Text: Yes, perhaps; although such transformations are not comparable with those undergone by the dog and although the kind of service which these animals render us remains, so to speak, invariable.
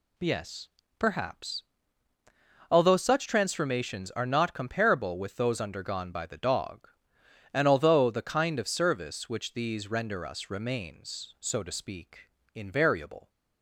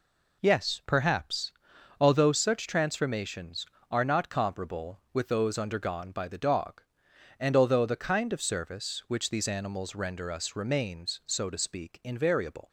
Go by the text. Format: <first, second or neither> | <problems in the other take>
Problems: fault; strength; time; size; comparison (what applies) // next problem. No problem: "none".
second | skips "animals"; at 9.8 s